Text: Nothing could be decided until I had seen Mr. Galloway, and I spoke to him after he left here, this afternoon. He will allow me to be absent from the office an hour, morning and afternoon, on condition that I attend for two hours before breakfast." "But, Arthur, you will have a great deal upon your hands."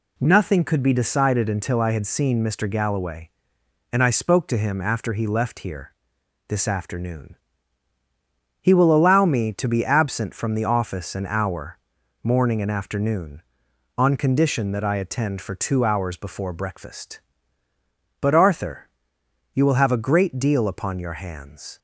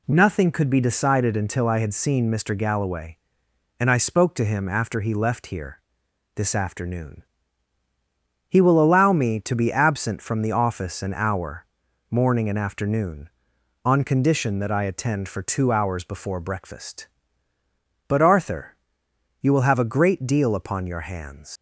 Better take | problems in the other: first | leaves "hands" unfinished; at 21.5 s; 100 ms

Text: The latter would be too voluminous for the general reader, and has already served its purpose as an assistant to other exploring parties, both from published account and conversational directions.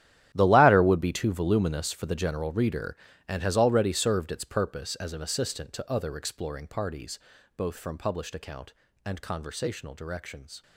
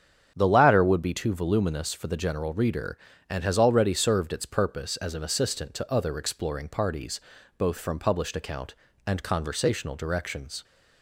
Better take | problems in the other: second | gets quieter; strong; throughout; 15.5 dB // starts louder than the rest; strong; until 1.3 s; 12 dB; strong in the second

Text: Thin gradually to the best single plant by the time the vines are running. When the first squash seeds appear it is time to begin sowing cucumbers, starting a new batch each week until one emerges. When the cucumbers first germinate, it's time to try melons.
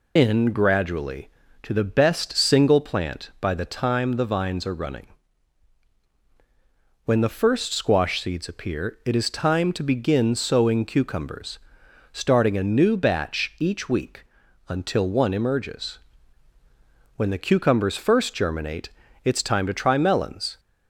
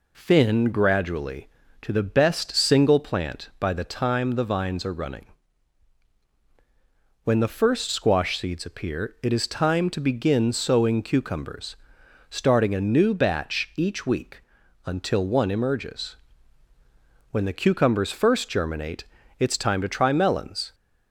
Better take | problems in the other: second | loses the start of "Thin"; at 0.1 s; 185 ms // pauses between "week" and "until"; noticeable; at 14.2 s; 0.46 s long; noticeable in the second

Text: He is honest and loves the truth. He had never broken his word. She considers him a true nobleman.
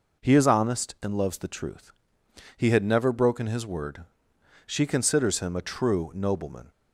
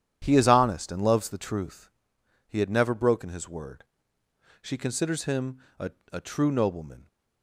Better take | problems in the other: first | starts louder than the rest; strong; until 1.2 s; 10 dB // pauses between "him" and "a"; slight; at 5.5 s; 0.22 s long // says "a" twice; at 6.1 s

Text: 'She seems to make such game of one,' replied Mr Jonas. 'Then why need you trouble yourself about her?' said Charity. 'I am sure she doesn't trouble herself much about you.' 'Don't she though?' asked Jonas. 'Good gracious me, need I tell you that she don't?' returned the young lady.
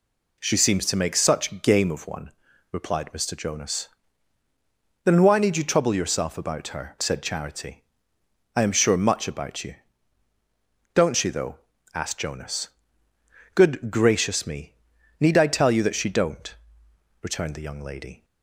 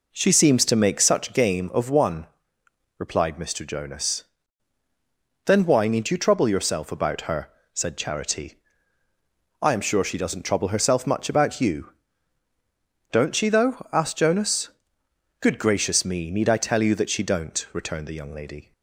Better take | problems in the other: second | skips "she doesn't trouble herself"; at 8.9 s

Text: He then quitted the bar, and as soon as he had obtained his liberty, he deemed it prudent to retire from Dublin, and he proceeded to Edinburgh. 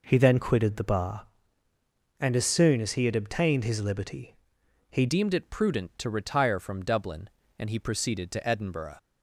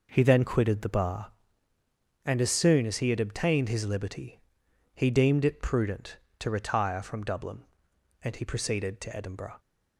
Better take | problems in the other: second | changes voice at "deemed"; from 5.0 s on; 3.9 s long

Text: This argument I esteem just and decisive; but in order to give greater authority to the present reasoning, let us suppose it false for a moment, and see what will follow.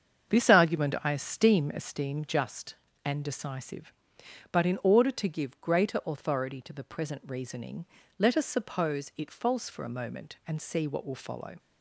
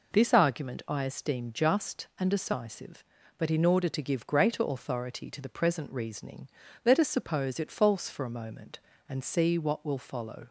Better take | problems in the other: second | starts louder than the rest; until 1.4 s; 7 dB // says "esteem" twice; at 1.7 s

